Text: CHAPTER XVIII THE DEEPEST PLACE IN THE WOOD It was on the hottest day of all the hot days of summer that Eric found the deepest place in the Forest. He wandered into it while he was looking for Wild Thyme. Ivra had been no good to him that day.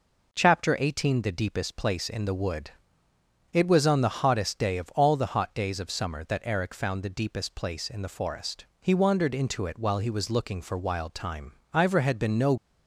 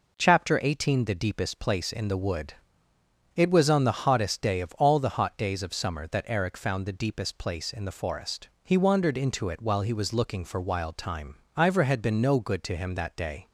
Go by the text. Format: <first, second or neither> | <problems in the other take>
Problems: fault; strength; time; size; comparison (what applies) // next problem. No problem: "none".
second | pauses between "WOOD" and "It"; noticeable; at 2.7 s; 0.80 s long; noticeable in the second // stops before "good to him that day"; at 12.5 s